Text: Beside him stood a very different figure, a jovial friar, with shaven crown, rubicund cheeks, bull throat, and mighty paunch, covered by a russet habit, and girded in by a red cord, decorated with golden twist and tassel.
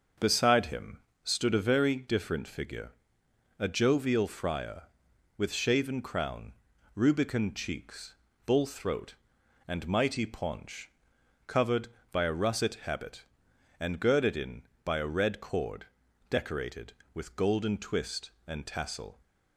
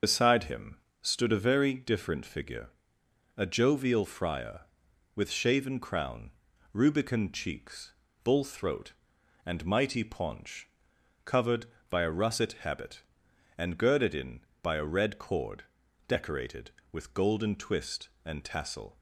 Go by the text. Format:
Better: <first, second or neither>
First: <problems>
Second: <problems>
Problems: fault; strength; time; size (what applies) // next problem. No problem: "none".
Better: first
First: starts louder than the rest; until 1.4 s; 6.5 dB // pauses between "him" and "stood"; slight; at 0.9 s; 0.24 s long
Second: loses the start of "Beside"; at 0.0 s; 75 ms // starts louder than the rest; until 1.2 s; 6.5 dB // pauses between "him" and "stood"; slight; at 0.7 s; 0.24 s long